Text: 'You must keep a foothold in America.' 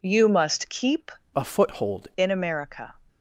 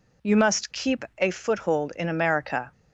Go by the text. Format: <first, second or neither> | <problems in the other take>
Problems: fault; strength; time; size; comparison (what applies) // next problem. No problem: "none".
second | changes voice from "a" to "foothold"; from 1.3 to 2.0 s; 0.7 s long